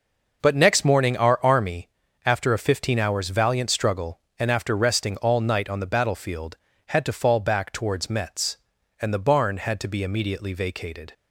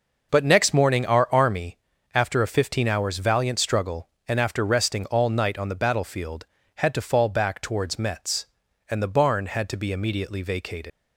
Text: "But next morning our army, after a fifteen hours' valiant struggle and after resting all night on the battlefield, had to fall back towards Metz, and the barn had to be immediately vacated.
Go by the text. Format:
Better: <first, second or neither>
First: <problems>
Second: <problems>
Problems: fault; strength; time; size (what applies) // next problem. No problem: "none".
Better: first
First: none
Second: leaves "vacated" unfinished; at 10.9 s; 120 ms